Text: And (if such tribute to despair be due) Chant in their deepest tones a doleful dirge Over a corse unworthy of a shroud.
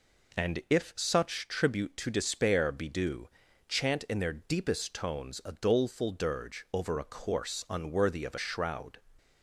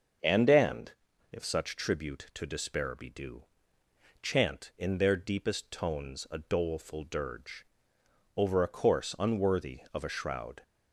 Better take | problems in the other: first | starts louder than the rest; until 1.6 s; 6.5 dB // says "And" twice; at 0.4 s // pauses between "dirge" and "Over"; noticeable; at 7.6 s; 0.70 s long

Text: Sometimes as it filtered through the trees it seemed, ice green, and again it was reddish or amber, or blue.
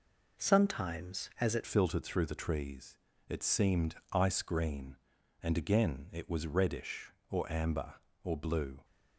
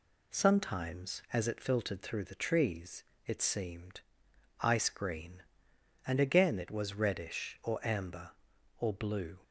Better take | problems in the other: second | changes voice at "filtered"; from 1.6 s on; 7.2 s long // pauses between "trees" and "it"; slight; at 2.9 s; 0.32 s long; slight in the second

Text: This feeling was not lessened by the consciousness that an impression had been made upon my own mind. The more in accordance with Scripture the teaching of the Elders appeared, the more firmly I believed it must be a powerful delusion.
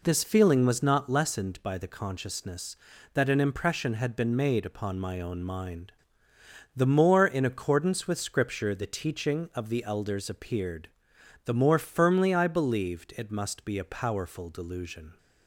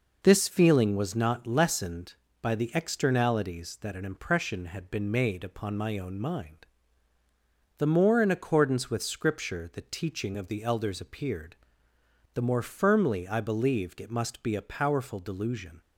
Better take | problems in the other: first | says "externalities" for "consciousness"; at 2.7 s

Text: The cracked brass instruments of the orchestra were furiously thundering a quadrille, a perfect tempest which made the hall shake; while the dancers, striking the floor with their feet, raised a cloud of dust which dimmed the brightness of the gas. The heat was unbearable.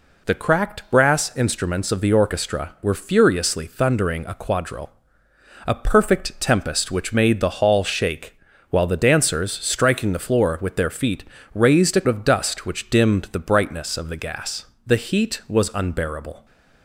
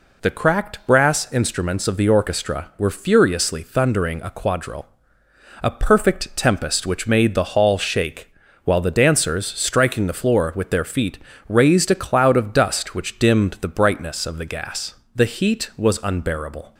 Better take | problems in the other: second | skips "cloud"; at 12.0 s

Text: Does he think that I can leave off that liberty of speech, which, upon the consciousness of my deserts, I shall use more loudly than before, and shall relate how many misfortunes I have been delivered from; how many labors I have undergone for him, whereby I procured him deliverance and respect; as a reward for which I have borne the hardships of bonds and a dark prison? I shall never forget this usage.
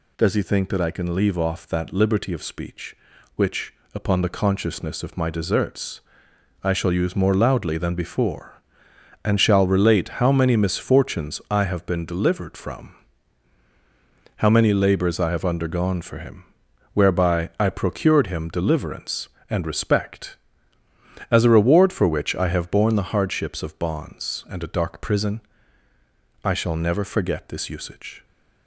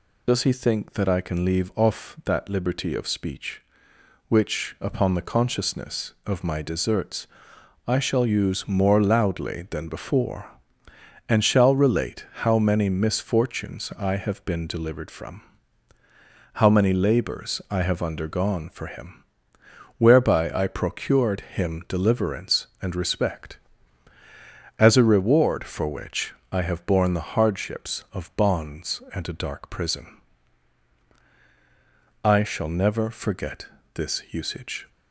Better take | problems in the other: first | loses the start of "Does"; at 0.2 s; 55 ms // pauses between "which" and "I"; slight; at 26.3 s; 0.18 s long // pauses between "forget" and "this"; slight; at 33.6 s; 0.28 s long

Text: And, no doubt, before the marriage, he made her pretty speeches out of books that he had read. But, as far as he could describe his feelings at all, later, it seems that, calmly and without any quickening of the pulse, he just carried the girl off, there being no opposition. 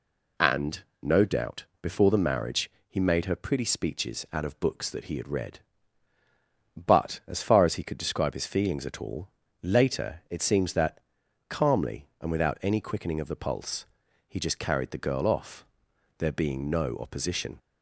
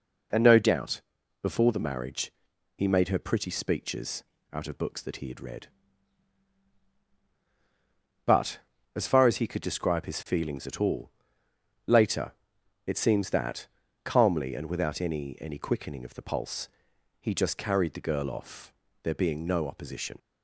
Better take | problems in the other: first | pauses between "speeches" and "out"; slight; at 4.2 s; 0.30 s long // says "any" twice; at 15.3 s

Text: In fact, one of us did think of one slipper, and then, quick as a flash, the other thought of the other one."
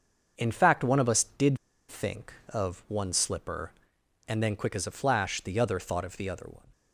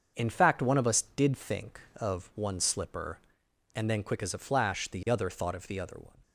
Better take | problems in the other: second | starts louder than the rest; until 1.3 s; 6.5 dB; also in the second // pauses between "did" and "think"; slight; at 1.5 s; 0.31 s long

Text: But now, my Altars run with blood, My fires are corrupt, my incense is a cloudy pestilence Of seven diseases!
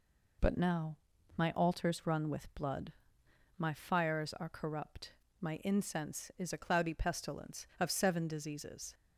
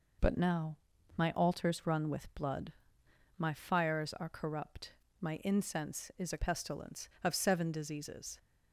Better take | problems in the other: first | skips "cloudy"; at 6.3 s

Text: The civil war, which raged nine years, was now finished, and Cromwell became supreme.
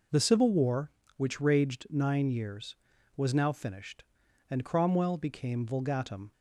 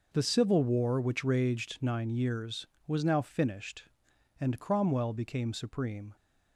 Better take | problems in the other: second | says "vulgatum" for "supreme"; at 5.6 s

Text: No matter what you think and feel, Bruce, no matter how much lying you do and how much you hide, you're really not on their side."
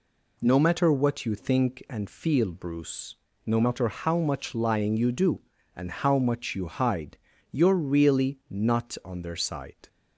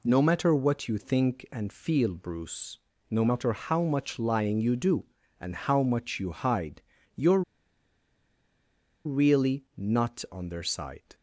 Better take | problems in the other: first | pauses between "you're" and "really"; strong; at 7.4 s; 1.6 s long

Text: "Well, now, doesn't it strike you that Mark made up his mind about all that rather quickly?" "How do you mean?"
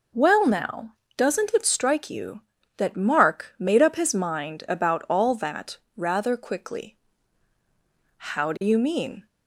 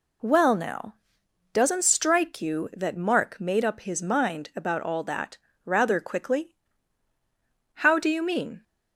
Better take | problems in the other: first | skips "it"; at 1.8 s // pauses between "that" and "rather"; slight; at 5.3 s; 0.25 s long; slight in the first

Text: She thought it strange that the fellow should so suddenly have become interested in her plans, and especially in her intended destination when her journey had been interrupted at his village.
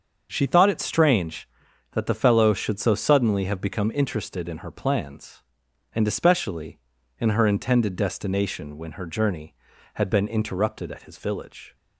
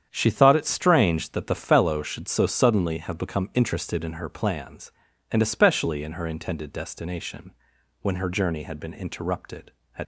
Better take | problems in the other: first | starts louder than the rest; strong; until 1.1 s; 8.5 dB; also in the first // pauses between "destination" and "when"; noticeable; at 7.5 s; 0.50 s long // stops before "his village"; at 10.0 s

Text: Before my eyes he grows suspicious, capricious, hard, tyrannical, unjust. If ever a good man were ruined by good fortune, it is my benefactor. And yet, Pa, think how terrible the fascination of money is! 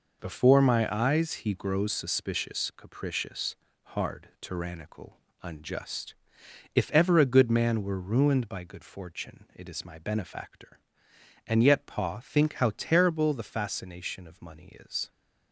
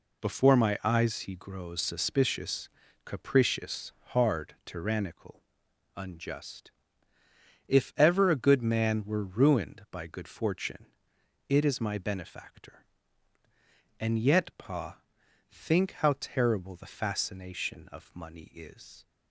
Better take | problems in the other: neither | none

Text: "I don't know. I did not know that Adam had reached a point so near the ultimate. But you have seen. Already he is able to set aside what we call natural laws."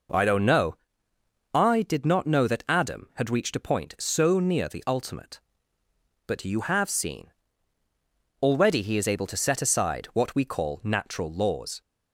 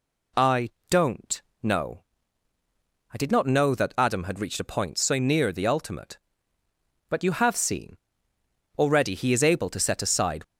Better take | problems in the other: first | pauses between "I" and "don't"; slight; at 0.7 s; 0.18 s long // pauses between "don't" and "know"; slight; at 1.4 s; 0.20 s long // stops before "what we call natural laws"; at 10.4 s

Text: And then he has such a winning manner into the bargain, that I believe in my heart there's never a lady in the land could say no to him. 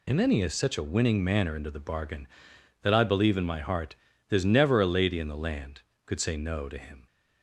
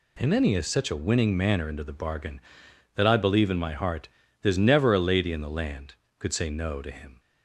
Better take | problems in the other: second | loses the start of "And"; at 0.0 s; 40 ms // pauses between "heart" and "there's"; slight; at 3.9 s; 0.34 s long; slight in the second

